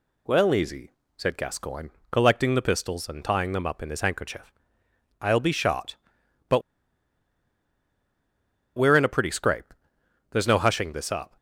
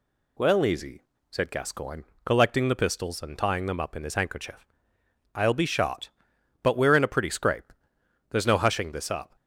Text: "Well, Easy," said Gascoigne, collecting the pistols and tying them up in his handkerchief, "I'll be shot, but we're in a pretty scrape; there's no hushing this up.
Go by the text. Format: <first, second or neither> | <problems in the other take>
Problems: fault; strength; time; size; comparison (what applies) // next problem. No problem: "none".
second | pauses between "but" and "we're"; strong; at 6.6 s; 2.1 s long